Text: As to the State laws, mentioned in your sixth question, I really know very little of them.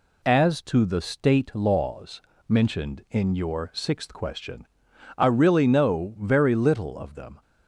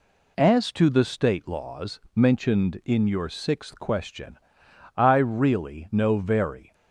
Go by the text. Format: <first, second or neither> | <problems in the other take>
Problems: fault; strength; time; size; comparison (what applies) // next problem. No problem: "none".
first | stops before "little of them"; at 6.7 s